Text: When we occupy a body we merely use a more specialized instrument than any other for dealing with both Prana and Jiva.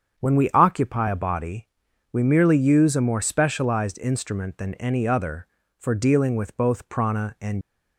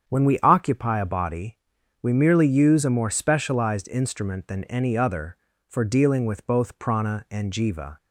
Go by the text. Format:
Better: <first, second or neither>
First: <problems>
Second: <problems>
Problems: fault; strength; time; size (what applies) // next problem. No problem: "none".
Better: second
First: starts louder than the rest; strong; until 1.2 s; 7.5 dB // pauses between "body" and "we"; at 1.6 s; 0.44 s long // stops before "Jiva"; at 7.6 s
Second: starts louder than the rest; strong; until 1.1 s; 8 dB // pauses between "body" and "we"; at 1.5 s; 0.44 s long